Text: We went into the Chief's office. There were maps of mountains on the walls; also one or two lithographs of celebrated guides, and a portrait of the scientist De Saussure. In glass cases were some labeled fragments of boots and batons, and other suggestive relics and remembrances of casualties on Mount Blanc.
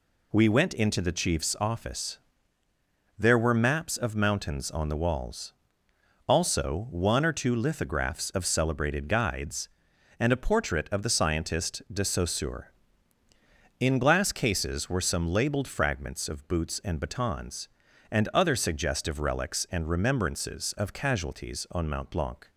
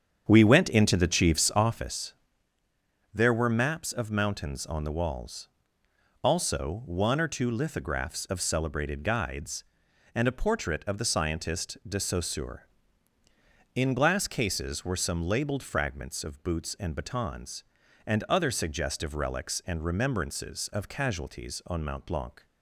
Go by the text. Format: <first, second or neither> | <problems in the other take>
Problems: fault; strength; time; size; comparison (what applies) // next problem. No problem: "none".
first | starts louder than the rest; strong; until 2.1 s; 8 dB